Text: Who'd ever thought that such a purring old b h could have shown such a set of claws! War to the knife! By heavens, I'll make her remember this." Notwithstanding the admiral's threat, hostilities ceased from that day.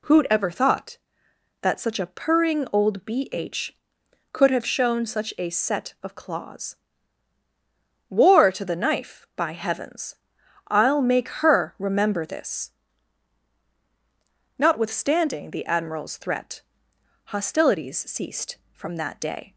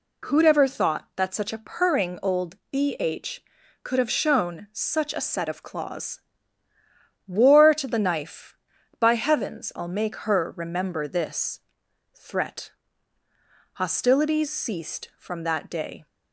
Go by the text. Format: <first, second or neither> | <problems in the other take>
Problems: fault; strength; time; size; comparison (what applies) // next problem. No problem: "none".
first | pauses between "old" and "b"; slight; at 2.5 s; 0.16 s long // skips "Notwithstanding the admiral's"; at 11.8 s